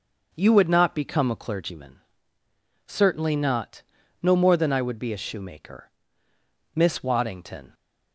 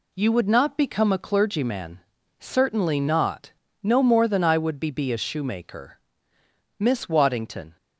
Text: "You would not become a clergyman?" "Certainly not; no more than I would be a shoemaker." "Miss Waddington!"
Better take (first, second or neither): first